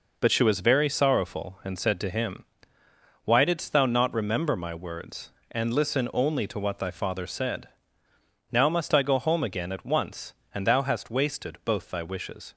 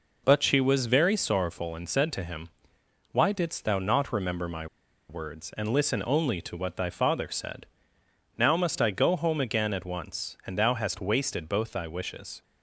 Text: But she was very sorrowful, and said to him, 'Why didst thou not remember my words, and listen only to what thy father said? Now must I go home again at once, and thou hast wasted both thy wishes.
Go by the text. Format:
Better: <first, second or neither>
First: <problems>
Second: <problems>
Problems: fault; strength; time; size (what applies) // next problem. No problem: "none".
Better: first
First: none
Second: pauses between "my" and "words"; at 4.6 s; 0.43 s long